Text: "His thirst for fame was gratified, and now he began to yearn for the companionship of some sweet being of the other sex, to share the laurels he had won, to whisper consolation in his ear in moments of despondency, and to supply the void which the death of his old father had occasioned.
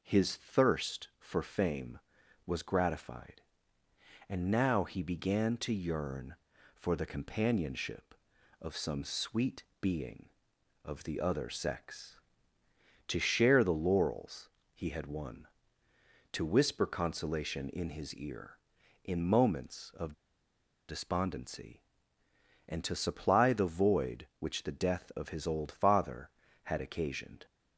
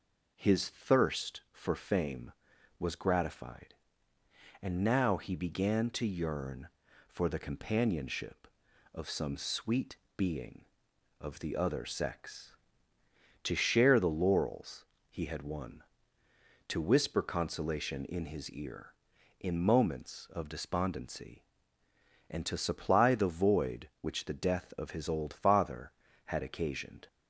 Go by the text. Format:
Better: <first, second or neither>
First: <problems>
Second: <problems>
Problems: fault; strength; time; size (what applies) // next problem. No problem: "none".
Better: second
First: pauses between "sweet" and "being"; slight; at 9.6 s; 0.16 s long // pauses between "laurels" and "he"; slight; at 14.4 s; 0.24 s long // pauses between "of" and "despondency"; noticeable; at 20.1 s; 0.75 s long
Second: pauses between "sweet" and "being"; slight; at 9.9 s; 0.19 s long // pauses between "laurels" and "he"; slight; at 14.8 s; 0.24 s long